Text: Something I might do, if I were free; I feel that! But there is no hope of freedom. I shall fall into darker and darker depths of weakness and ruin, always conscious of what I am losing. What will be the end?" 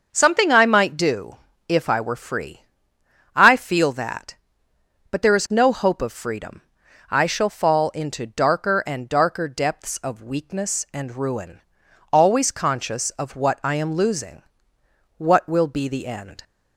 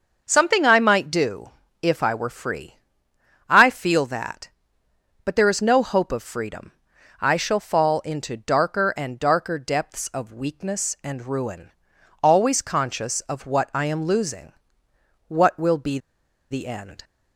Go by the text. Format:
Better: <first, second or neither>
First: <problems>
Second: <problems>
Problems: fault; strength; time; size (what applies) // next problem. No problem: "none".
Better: first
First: starts louder than the rest; noticeable; until 1.1 s; 6 dB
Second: starts louder than the rest; noticeable; until 1.2 s; 6 dB // pauses between "be" and "the"; noticeable; at 15.9 s; 0.53 s long